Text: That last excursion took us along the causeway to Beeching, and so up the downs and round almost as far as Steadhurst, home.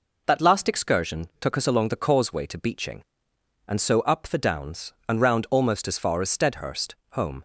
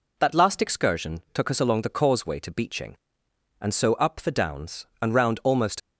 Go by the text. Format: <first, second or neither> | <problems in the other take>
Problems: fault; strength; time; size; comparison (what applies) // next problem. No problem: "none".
first | stops before "as far as Steadhurst home"; at 5.7 s